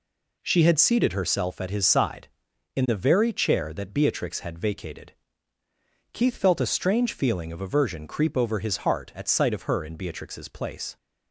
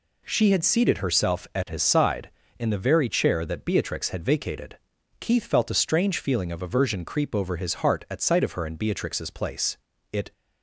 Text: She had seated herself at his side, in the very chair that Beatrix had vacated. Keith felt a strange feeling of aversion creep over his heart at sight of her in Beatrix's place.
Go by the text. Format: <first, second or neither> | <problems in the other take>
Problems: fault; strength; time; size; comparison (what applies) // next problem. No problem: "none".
first | goes on to say "It"; slight; from 10.1 s on; 0.20 s long